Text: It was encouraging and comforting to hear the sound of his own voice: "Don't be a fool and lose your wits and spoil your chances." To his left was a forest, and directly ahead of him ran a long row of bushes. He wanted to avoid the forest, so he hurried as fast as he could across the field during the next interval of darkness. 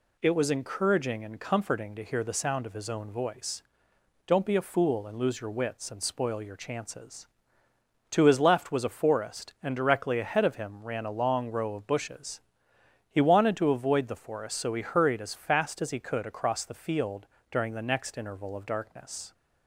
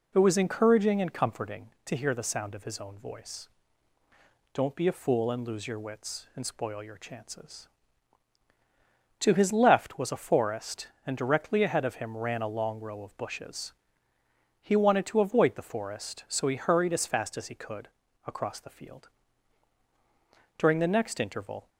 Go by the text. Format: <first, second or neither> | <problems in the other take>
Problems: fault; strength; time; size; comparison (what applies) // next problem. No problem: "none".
first | pauses between "could" and "across"; slight; at 17.8 s; 0.36 s long // pauses between "field" and "during"; strong; at 19.0 s; 1.4 s long; slight in the first // stops before "of darkness"; at 21.6 s